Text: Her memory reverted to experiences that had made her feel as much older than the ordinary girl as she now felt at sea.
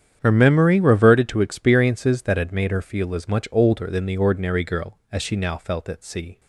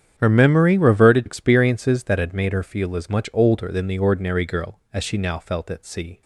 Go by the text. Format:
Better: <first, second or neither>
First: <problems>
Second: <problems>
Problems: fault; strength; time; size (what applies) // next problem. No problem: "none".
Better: first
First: starts louder than the rest; strong; until 1.2 s; 9 dB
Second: starts louder than the rest; strong; until 1.1 s; 9 dB // skips "to"; at 1.2 s